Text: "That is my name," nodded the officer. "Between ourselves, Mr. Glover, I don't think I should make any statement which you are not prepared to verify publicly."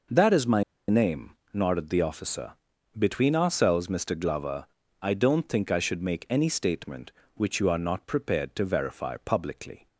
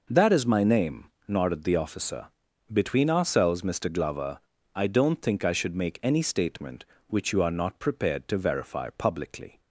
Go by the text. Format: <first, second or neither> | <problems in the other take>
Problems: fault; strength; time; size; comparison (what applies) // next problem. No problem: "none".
second | pauses between "my" and "name"; slight; at 0.6 s; 0.27 s long